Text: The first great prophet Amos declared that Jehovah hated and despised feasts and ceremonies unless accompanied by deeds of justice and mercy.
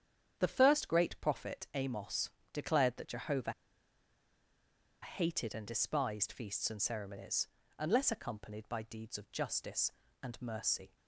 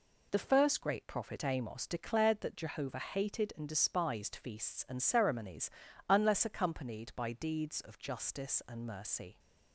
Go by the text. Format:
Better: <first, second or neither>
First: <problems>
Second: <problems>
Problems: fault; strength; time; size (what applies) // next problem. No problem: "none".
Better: second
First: starts louder than the rest; strong; until 1.3 s; 8.5 dB // pauses between "Amos" and "declared"; slight; at 2.2 s; 0.24 s long // pauses between "Jehovah" and "hated"; strong; at 3.5 s; 1.4 s long // pauses between "ceremonies" and "unless"; slight; at 7.4 s; 0.32 s long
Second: pauses between "ceremonies" and "unless"; slight; at 5.7 s; 0.36 s long